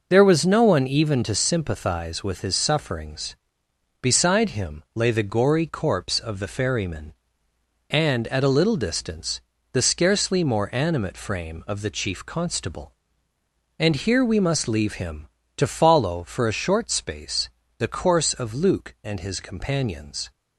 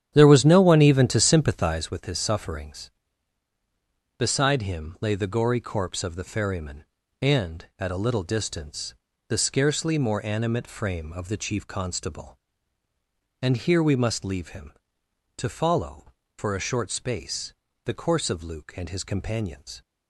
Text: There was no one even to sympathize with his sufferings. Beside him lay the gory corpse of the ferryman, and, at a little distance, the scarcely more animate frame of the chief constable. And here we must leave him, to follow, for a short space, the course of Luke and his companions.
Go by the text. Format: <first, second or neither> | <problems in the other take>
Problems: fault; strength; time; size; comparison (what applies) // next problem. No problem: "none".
first | starts louder than the rest; strong; until 2.0 s; 9.5 dB